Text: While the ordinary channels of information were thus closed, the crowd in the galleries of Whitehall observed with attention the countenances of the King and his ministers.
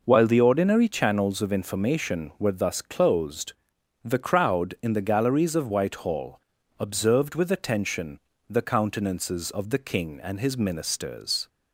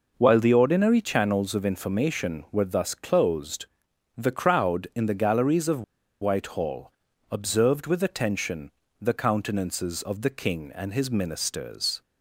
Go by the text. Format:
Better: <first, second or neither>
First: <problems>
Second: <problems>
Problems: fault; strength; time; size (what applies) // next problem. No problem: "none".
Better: first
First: pauses between "Whitehall" and "observed"; at 6.3 s; 0.40 s long // pauses between "attention" and "the"; slight; at 8.1 s; 0.32 s long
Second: pauses between "of" and "Whitehall"; at 5.8 s; 0.39 s long // pauses between "Whitehall" and "observed"; at 6.9 s; 0.40 s long // pauses between "attention" and "the"; slight; at 8.6 s; 0.32 s long